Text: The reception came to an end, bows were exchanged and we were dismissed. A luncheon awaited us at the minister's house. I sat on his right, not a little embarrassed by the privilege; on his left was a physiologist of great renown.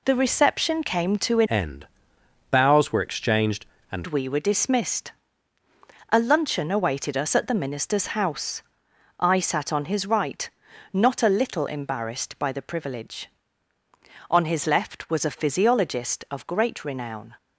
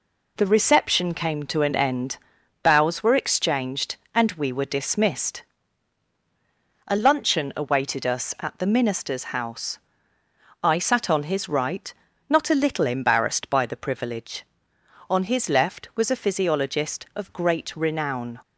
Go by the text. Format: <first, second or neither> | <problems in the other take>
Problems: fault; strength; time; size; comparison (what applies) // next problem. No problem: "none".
second | changes voice from "end" to "and"; from 1.4 to 4.0 s; 2.6 s long